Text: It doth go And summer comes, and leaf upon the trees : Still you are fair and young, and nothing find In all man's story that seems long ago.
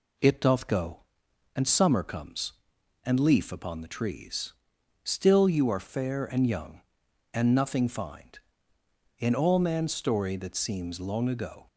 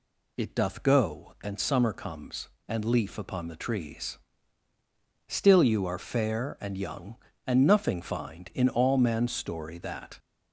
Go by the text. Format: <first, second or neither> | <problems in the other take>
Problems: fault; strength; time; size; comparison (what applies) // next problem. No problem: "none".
first | stops before "seems long ago"; at 10.1 s